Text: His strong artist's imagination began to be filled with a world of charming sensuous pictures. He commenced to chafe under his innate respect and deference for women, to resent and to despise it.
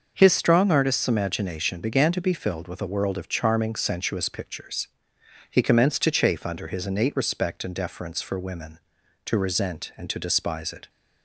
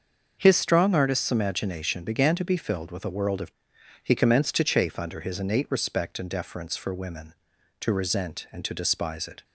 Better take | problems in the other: first | starts louder than the rest; until 1.4 s; 6.5 dB; also in the first // skips "charming sensuous pictures"; at 3.7 s

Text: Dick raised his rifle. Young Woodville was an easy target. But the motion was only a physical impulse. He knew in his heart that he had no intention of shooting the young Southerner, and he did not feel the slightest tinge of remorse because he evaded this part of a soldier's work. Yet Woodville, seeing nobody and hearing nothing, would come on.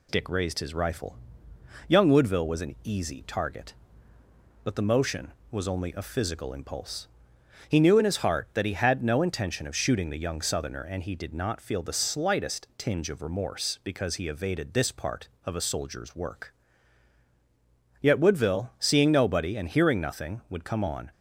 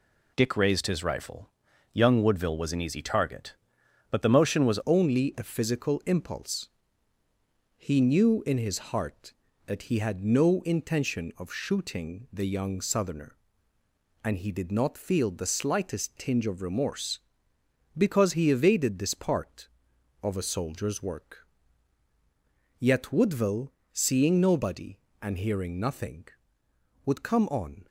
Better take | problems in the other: first | changes voice at "only"; from 4.8 s on; 23.0 s long

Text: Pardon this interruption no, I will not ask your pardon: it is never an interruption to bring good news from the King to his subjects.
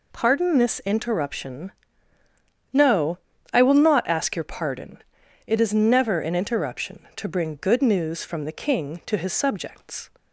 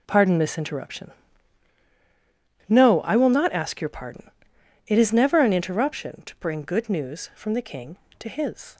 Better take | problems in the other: first | pauses between "interruption" and "no"; strong; at 1.1 s; 1.5 s long; also in the first // stops before "subjects"; at 8.7 s

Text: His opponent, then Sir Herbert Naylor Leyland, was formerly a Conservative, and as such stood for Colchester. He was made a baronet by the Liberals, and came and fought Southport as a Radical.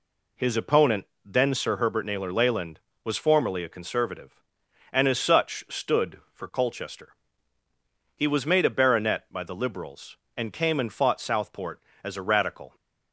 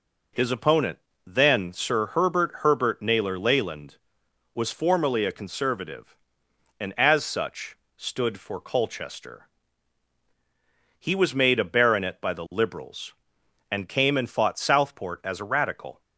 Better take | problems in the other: first | says "Herbert" twice; at 2.6 s // pauses between "such" and "stood"; slight; at 7.7 s; 0.20 s long

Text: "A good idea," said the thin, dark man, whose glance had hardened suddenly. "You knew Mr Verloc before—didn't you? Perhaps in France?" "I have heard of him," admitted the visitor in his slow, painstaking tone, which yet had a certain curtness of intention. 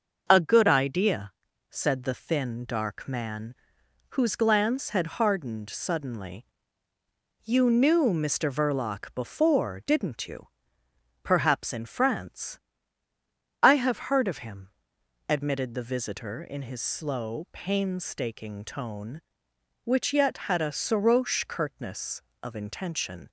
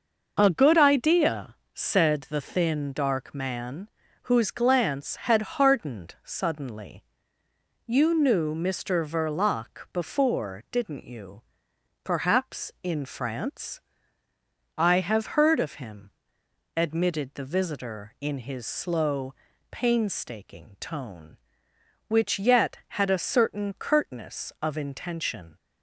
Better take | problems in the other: second | starts louder than the rest; until 1.2 s; 6.5 dB // says "soroche" for "certain"; at 20.7 s

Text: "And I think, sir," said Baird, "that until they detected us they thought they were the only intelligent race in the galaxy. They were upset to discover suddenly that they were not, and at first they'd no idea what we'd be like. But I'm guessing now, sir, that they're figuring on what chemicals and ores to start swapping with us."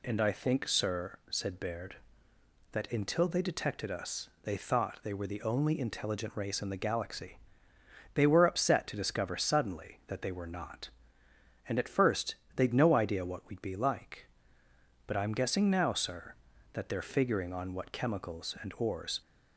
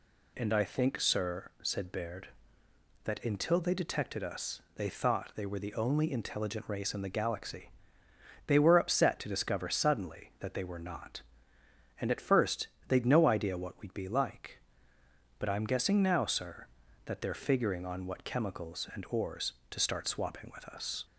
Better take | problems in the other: second | pauses between "first" and "they'd"; slight; at 12.3 s; 0.18 s long; slight in the second // stops before "to start swapping with us"; at 19.2 s

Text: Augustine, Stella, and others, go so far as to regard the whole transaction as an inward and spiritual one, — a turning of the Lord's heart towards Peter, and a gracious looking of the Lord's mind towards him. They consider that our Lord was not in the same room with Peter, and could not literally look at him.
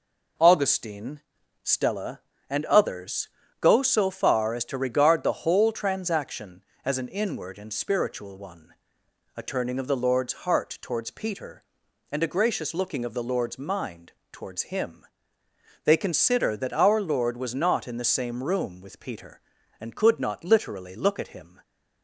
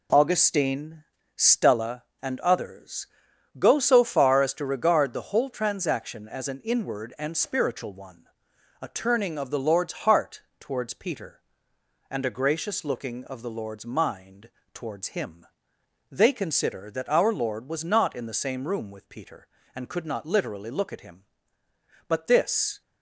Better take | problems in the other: first | pauses between "heart" and "towards"; slight; at 10.4 s; 0.18 s long // pauses between "mind" and "towards"; slight; at 14.4 s; 0.24 s long; slight in the first // goes on to say "But this"; noticeable; from 22.0 s on; 0.72 s long

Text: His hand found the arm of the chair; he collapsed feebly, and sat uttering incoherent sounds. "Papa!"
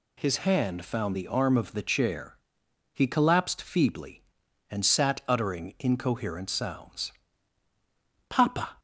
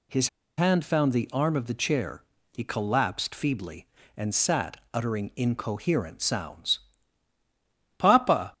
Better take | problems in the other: first | pauses between "His" and "hand"; slight; at 0.2 s; 0.29 s long // pauses between "sat" and "uttering"; slight; at 4.7 s; 0.18 s long

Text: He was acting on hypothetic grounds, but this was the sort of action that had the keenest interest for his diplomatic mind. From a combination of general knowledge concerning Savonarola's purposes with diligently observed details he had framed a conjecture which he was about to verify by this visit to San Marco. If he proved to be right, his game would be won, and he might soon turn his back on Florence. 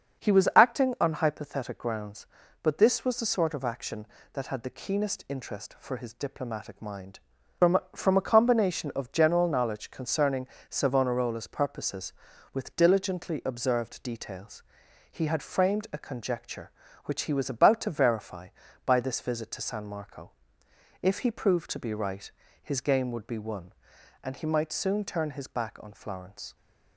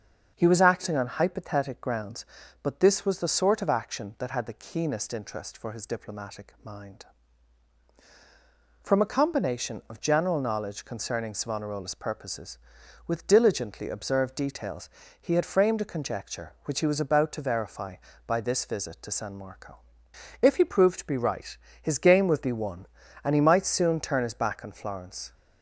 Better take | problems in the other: second | starts louder than the rest; until 1.3 s; 6.5 dB; also in the second // says "From" twice; at 7.9 s // pauses between "concerning" and "Savonarola's"; slight; at 10.4 s; 0.20 s long // pauses between "details" and "he"; noticeable; at 14.6 s; 0.48 s long; slight in the second

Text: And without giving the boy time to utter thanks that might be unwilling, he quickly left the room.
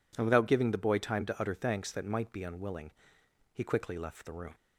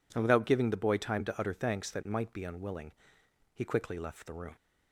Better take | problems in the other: neither | none

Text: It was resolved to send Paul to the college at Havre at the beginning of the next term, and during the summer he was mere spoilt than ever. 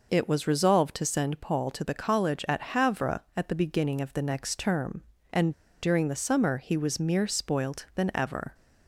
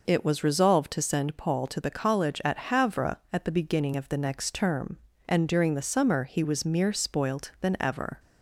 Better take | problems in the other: second | pauses between "and" and "during"; slight; at 5.5 s; 0.29 s long

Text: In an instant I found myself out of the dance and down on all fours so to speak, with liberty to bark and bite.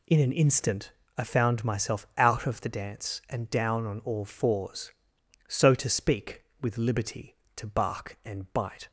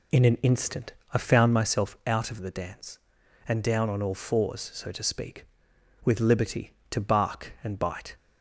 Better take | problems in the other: first | starts louder than the rest; slight; until 1.7 s; 2.5 dB // pauses between "instant" and "I"; slight; at 0.9 s; 0.20 s long; slight in the first

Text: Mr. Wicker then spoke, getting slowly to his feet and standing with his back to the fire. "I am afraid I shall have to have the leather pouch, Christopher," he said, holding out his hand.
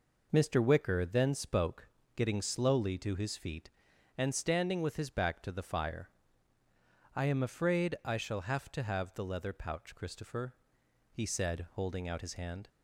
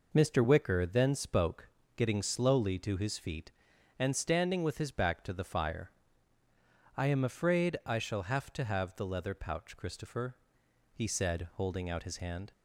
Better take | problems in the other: neither | none

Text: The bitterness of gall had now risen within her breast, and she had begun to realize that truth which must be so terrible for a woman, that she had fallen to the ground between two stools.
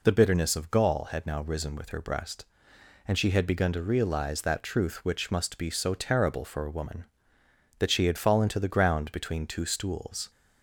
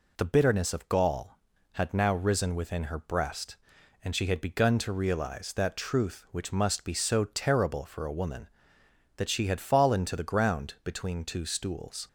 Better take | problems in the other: second | says "with" for "within"; at 1.7 s

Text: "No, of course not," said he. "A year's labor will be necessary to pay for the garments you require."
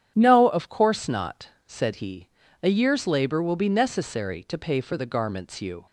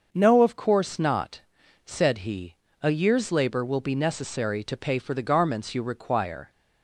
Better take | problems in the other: second | starts louder than the rest; strong; until 1.1 s; 9.5 dB; also in the second // stops before "require"; at 5.8 s

